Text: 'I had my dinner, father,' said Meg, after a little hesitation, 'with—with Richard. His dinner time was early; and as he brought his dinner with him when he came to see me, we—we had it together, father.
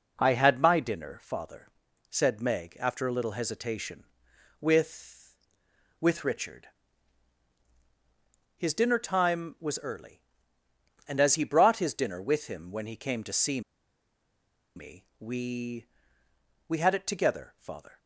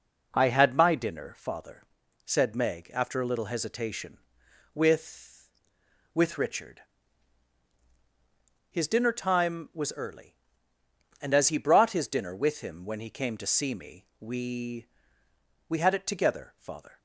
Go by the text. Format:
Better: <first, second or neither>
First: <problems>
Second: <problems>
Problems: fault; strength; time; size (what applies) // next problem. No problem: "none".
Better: second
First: pauses between "see" and "me"; at 13.5 s; 1.1 s long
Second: none